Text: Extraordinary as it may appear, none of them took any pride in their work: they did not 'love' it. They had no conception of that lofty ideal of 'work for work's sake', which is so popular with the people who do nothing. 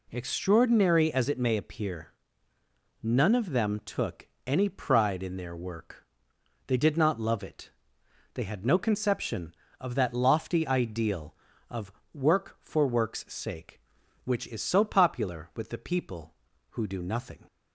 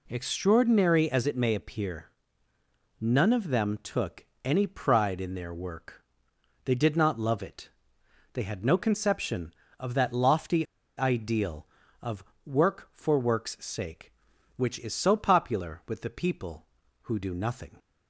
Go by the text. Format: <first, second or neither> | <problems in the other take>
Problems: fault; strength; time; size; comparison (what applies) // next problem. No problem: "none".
first | pauses between "took" and "any"; slight; at 4.2 s; 0.20 s long; slight in the first // pauses between "lofty" and "ideal"; slight; at 10.6 s; 0.32 s long // pauses between "of" and "work"; slight; at 12.2 s; 0.22 s long; slight in the first